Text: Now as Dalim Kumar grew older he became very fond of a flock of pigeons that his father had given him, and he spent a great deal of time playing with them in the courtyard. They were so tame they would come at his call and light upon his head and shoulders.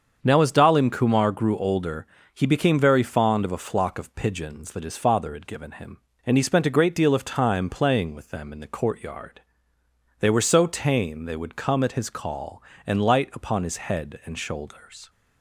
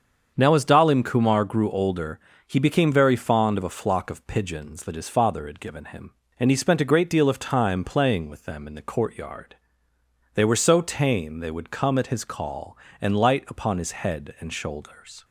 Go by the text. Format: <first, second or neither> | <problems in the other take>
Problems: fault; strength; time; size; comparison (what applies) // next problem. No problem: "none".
neither | starts louder than the rest; the same in both // pauses between "older" and "he"; slight; the same in both